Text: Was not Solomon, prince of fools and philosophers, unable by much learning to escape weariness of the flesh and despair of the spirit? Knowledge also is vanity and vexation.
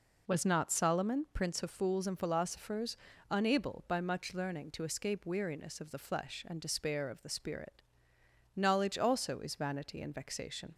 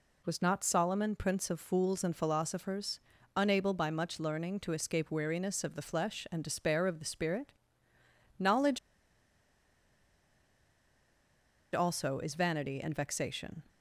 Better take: first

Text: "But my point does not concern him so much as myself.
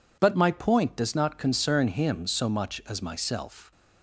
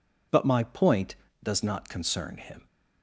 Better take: first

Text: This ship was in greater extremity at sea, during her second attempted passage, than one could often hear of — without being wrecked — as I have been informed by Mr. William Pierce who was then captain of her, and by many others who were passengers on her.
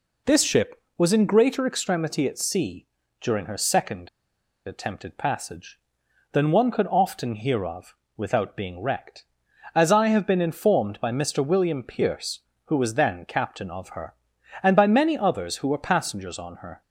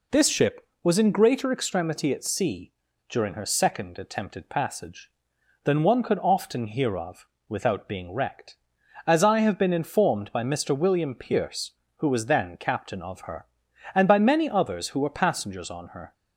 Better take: second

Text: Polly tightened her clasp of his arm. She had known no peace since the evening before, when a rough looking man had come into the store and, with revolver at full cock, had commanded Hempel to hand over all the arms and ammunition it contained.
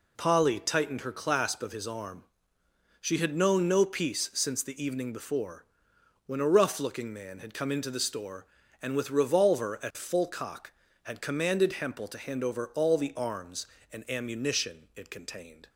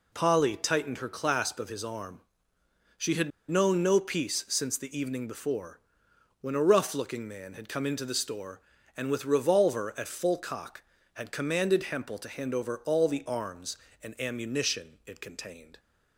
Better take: first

